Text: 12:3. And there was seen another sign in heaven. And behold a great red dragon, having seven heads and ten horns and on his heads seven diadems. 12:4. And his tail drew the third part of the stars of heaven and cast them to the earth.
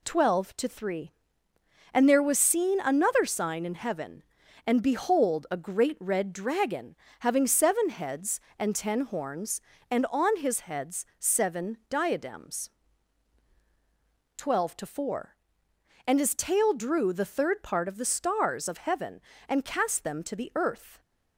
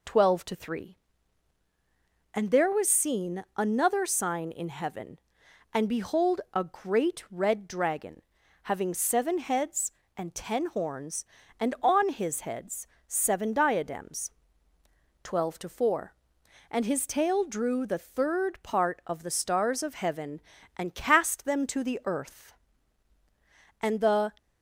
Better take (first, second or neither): first